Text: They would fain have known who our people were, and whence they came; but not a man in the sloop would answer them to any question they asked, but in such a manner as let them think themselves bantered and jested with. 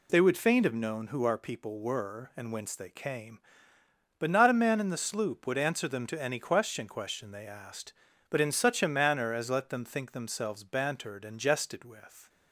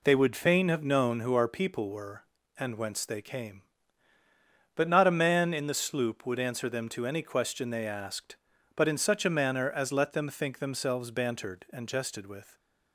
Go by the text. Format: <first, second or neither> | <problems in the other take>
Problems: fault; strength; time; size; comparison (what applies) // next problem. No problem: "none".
second | says "question" twice; at 6.8 s